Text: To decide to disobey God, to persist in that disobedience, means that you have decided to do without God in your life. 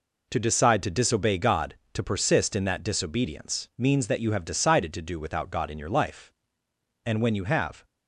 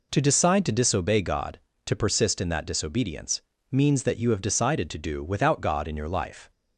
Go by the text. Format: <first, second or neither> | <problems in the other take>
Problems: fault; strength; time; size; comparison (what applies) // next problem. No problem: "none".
second | goes on to say "And when you have"; noticeable; from 7.0 s on; 0.80 s long